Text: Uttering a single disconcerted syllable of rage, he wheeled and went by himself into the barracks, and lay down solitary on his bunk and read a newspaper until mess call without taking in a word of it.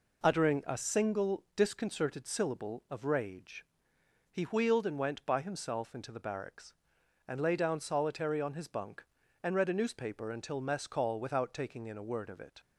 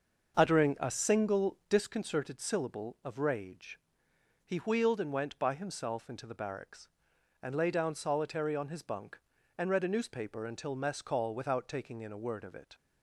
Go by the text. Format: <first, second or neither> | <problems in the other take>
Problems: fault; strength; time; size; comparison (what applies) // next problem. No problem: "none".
first | starts louder than the rest; until 1.8 s; 6.5 dB